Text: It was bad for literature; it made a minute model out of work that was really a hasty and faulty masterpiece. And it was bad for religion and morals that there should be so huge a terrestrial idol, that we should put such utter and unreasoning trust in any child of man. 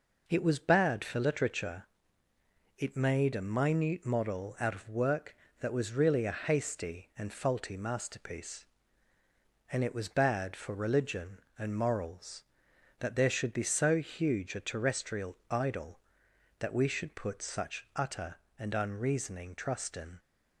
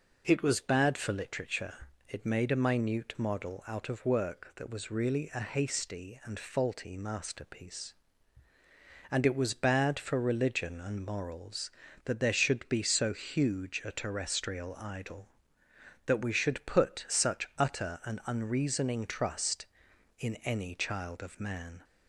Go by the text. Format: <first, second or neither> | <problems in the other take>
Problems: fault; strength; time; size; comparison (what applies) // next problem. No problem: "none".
second | stops before "any child of man"; at 20.1 s